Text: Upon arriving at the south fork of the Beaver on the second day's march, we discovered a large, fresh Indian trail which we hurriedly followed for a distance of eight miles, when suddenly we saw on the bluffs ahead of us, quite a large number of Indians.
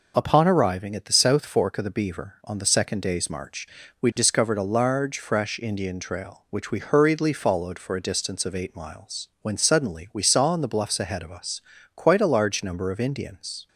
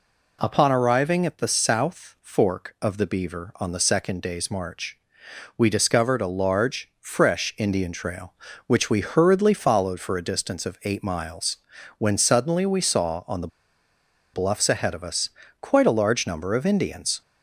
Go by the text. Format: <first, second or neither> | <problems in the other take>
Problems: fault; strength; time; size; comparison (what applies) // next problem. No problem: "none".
first | pauses between "the" and "bluffs"; noticeable; at 13.4 s; 0.86 s long